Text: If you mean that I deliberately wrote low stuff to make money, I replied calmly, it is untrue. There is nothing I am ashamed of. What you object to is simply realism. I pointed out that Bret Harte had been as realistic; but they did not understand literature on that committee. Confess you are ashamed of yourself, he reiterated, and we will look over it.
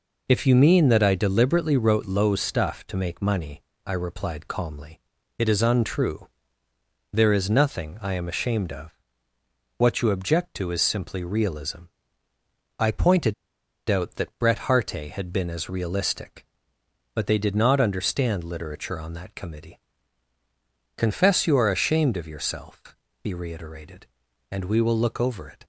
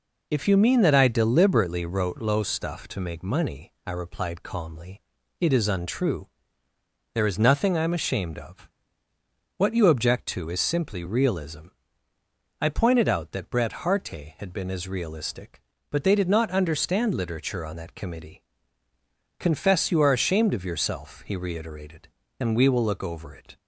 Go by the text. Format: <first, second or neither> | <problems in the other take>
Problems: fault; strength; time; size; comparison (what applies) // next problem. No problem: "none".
second | pauses between "pointed" and "out"; noticeable; at 13.3 s; 0.54 s long